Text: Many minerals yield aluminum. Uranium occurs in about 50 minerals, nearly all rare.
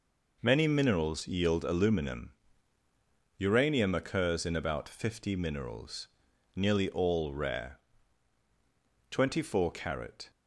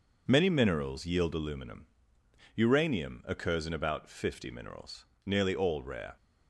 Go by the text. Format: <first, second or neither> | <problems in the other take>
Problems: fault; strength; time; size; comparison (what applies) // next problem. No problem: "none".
second | goes on to say "Twenty four carat"; noticeable; from 9.1 s on; 1.2 s long